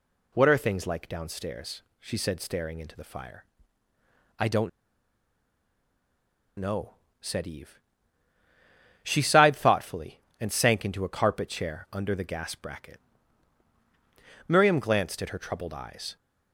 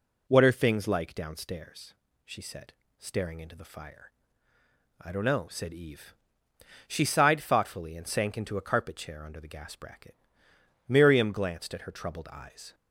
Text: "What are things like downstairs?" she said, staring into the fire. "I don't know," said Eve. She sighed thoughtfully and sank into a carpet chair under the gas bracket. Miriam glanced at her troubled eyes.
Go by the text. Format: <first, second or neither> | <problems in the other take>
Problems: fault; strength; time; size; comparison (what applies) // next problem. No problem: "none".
second | pauses between "don't" and "know"; strong; at 4.6 s; 1.8 s long